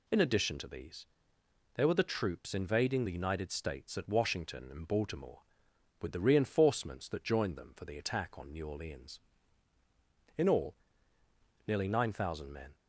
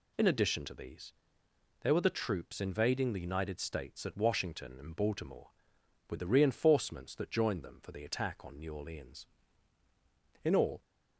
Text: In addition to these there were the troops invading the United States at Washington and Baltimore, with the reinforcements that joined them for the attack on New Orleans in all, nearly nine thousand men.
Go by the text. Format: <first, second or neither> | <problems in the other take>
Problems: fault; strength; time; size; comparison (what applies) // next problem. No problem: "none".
first | pauses between "these" and "there"; noticeable; at 1.1 s; 0.70 s long; noticeable in the first // stops before "nearly nine thousand men"; at 10.8 s